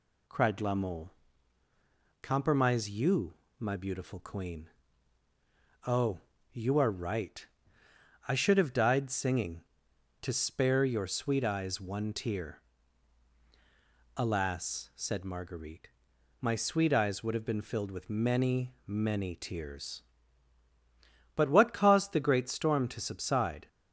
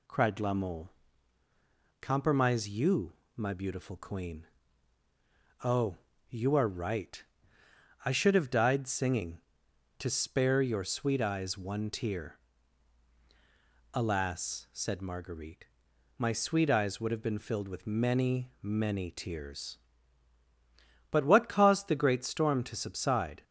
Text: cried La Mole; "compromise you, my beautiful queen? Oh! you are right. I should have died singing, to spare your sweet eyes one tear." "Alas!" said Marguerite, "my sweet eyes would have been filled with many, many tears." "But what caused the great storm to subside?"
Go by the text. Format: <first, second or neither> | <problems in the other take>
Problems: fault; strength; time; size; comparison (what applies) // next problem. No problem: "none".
neither | none